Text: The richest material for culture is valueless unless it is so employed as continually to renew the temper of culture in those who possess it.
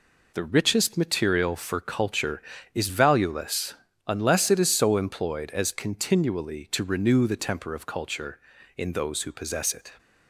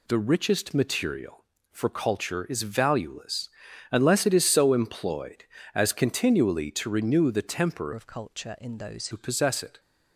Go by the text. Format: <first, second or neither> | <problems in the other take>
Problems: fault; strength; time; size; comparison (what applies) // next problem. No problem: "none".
first | pauses between "valueless" and "unless"; at 3.4 s; 0.42 s long; slight in the first // changes voice from "of" to "those"; from 7.9 to 9.0 s; 1.1 s long